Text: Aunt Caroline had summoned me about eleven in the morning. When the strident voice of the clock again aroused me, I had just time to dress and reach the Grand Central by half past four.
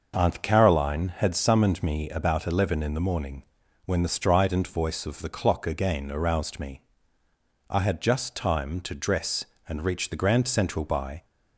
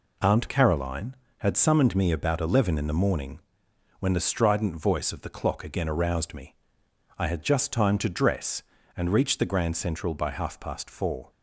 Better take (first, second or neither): second